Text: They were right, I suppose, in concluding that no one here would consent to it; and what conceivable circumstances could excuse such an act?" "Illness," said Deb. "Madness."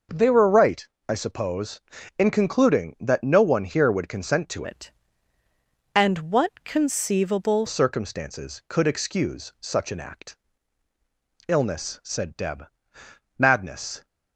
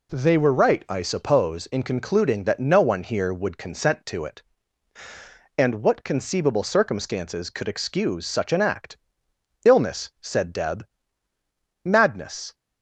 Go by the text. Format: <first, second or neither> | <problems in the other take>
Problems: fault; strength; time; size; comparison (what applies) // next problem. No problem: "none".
second | changes voice from "it" to "conceivable"; from 4.6 to 7.6 s; 3.0 s long